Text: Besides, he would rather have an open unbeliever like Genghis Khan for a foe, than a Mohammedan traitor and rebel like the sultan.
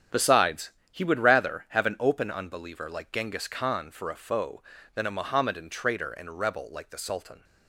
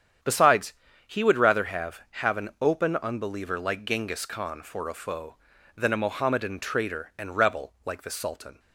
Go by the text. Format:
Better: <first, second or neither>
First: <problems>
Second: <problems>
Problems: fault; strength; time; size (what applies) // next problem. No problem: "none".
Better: first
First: starts louder than the rest; strong; until 1.3 s; 9 dB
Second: starts louder than the rest; strong; until 1.5 s; 8.5 dB // says "have" twice; at 2.1 s